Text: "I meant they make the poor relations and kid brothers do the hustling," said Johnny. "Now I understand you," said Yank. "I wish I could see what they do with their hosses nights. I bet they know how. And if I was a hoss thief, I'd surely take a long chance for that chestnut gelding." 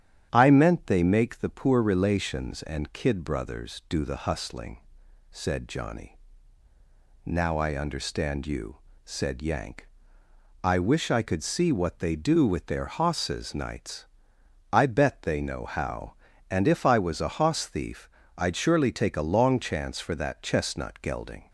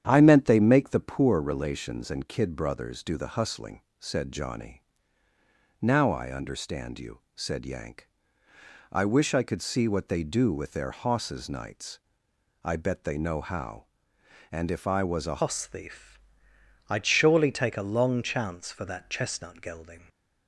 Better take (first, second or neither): first